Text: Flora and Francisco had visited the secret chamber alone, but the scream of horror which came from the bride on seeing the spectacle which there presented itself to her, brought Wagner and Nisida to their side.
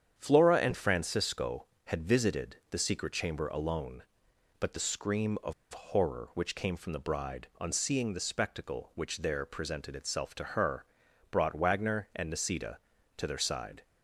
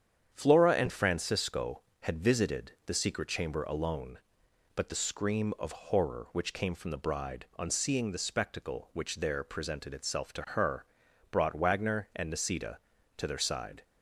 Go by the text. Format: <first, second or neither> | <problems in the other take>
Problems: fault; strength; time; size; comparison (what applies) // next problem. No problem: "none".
second | starts louder than the rest; strong; until 1.1 s; 8.5 dB; strong in the second // pauses between "of" and "horror"; slight; at 5.5 s; 0.20 s long